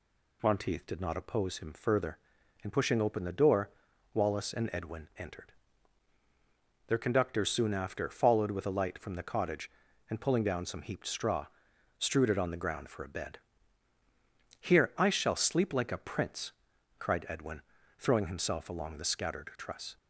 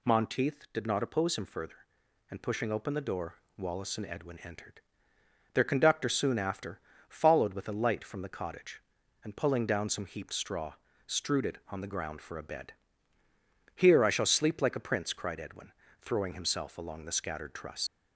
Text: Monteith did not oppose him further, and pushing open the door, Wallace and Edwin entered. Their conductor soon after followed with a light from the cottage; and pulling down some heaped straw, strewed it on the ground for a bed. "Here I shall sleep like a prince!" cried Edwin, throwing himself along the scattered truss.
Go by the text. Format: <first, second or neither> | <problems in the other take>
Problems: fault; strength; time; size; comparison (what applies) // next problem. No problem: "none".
first | pauses between "after" and "followed"; slight; at 6.7 s; 0.28 s long // leaves "truss" unfinished; at 17.8 s; 60 ms